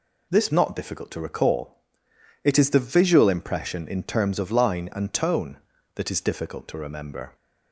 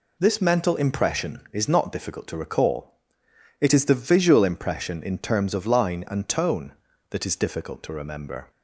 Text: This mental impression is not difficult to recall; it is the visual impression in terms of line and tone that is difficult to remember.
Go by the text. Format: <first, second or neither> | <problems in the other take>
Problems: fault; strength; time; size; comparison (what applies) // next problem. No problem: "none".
second | skips "mental impression is"; at 0.5 s